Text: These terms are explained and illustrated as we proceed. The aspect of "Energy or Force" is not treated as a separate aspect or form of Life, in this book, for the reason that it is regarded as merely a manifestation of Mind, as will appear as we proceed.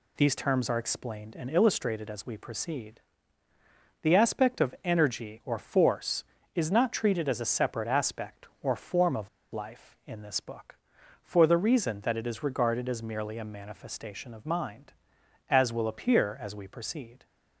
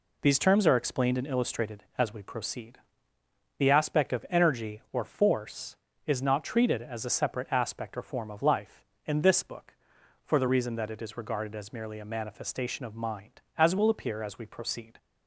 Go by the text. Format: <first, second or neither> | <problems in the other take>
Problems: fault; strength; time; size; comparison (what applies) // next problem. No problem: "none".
second | pauses between "of" and "Life"; slight; at 9.2 s; 0.23 s long